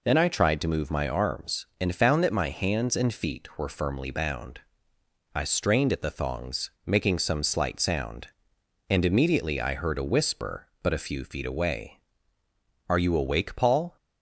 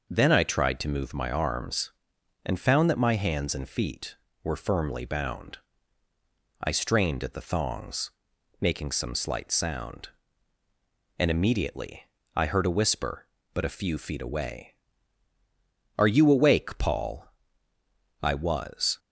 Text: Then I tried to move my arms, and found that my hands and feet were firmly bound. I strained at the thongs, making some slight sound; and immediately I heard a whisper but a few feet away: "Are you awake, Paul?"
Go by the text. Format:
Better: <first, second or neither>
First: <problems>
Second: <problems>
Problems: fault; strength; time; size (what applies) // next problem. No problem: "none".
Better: first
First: none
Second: pauses between "immediately" and "I"; slight; at 12.0 s; 0.32 s long // goes on to say "I was"; noticeable; from 18.2 s on; 0.78 s long